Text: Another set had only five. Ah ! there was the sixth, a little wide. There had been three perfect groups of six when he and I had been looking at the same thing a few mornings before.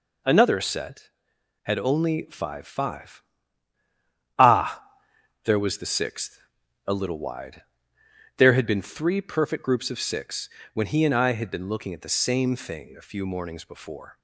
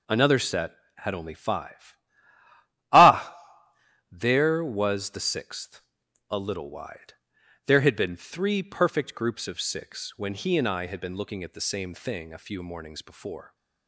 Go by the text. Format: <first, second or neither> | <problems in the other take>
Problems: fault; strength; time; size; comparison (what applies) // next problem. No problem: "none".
second | says "five" twice; at 2.6 s // pauses between "six" and "when"; slight; at 10.4 s; 0.26 s long